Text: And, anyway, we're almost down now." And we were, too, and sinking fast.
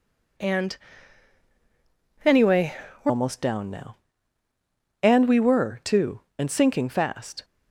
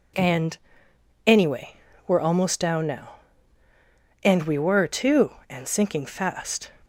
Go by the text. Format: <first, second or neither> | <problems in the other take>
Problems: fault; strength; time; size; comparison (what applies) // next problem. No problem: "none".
second | changes voice at "almost"; from 3.0 s on; 4.4 s long